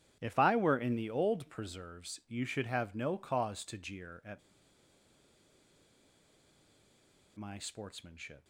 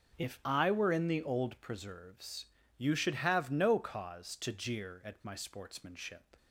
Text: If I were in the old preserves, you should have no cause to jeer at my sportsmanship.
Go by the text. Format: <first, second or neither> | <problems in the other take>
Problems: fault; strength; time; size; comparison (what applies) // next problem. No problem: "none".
second | starts louder than the rest; strong; until 1.2 s; 10 dB; noticeable in the second // pauses between "at" and "my"; strong; at 4.4 s; 2.9 s long